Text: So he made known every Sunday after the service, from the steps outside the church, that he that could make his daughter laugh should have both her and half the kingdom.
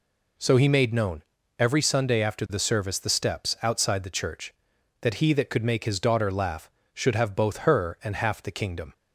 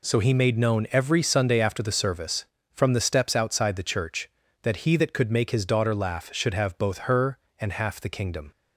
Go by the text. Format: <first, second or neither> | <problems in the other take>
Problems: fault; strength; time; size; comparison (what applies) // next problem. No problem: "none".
second | pauses between "known" and "every"; slight; at 1.2 s; 0.36 s long // skips "from"; at 2.9 s